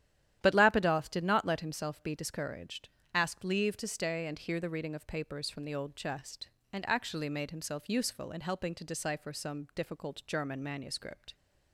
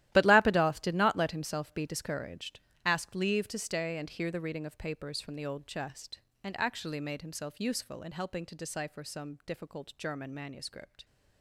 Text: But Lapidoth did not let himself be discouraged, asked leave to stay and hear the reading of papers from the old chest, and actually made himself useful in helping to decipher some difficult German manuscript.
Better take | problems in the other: first | gets quieter; strong; throughout; 13.5 dB // starts louder than the rest; strong; until 1.1 s; 14 dB; strong in the first

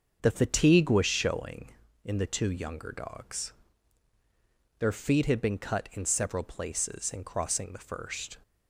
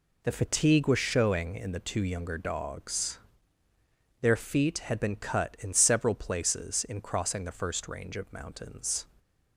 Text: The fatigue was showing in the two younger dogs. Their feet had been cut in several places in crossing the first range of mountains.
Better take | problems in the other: second | starts louder than the rest; until 1.2 s; 6.5 dB // stops before "range of mountains"; at 8.4 s

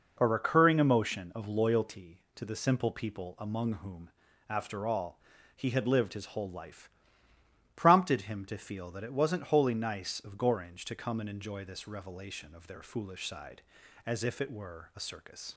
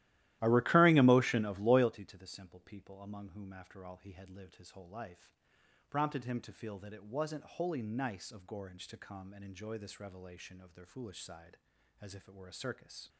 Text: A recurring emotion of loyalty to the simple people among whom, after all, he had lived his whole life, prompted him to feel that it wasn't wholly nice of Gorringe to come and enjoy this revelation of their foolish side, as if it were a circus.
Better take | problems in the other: first | starts louder than the rest; strong; until 1.9 s; 15 dB

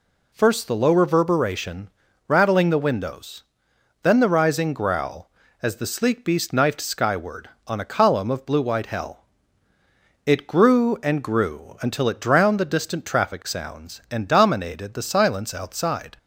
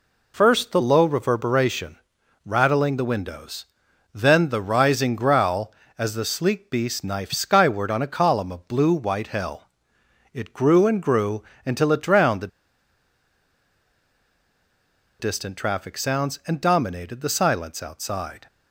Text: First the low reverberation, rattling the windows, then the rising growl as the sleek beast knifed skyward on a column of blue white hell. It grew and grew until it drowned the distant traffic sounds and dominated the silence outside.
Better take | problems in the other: first | pauses between "grew" and "until"; slight; at 11.4 s; 0.24 s long // pauses between "the" and "distant"; strong; at 12.4 s; 2.7 s long

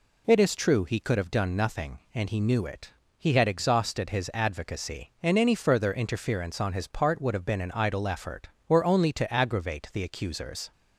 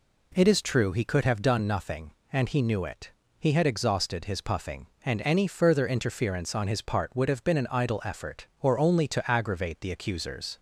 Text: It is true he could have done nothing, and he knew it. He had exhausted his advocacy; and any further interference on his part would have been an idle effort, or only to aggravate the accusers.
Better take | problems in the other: first | says "puffing" for "advocacy"; at 4.4 s

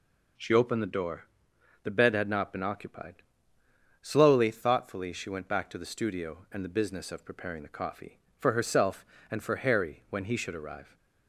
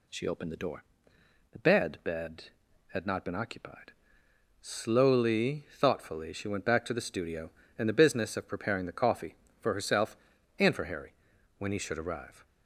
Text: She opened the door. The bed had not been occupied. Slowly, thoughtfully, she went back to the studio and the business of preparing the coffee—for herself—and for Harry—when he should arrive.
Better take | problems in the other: first | says "bed" twice; at 2.0 s

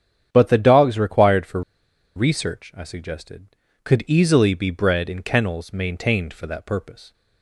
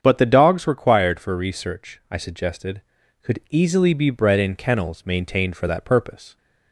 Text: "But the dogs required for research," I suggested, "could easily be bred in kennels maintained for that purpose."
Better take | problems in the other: second | starts louder than the rest; strong; until 1.3 s; 8.5 dB; strong in the second // pauses between "for" and "research"; noticeable; at 1.6 s; 0.55 s long

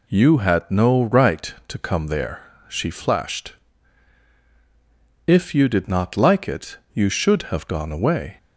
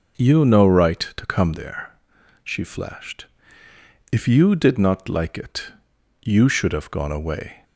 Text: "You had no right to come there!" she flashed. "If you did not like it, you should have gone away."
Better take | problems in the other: first | skips "had"; at 0.4 s

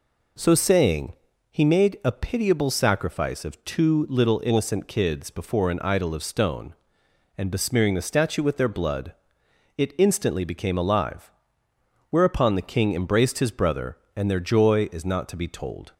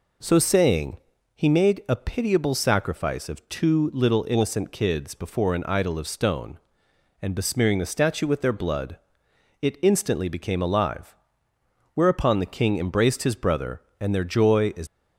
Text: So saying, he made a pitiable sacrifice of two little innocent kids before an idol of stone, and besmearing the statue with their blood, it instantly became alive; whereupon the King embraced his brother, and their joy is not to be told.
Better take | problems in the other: first | stops before "not to be told"; at 14.8 s

